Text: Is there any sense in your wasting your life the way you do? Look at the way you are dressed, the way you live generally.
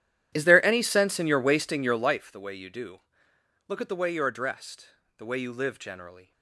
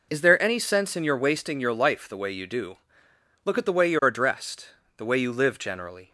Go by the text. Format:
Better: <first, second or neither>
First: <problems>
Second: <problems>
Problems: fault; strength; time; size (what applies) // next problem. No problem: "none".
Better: second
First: starts louder than the rest; strong; until 2.3 s; 11.5 dB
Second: none